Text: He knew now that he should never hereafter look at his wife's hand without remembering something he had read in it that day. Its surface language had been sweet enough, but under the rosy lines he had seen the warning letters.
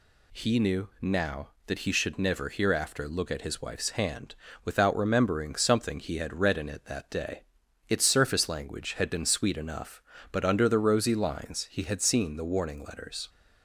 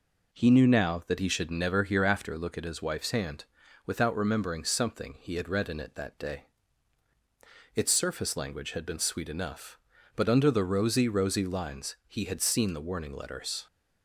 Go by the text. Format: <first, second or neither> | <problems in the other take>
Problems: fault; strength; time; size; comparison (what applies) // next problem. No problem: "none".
first | pauses between "hand" and "without"; at 3.4 s; 0.40 s long; slight in the first // says "rosy" twice; at 11.0 s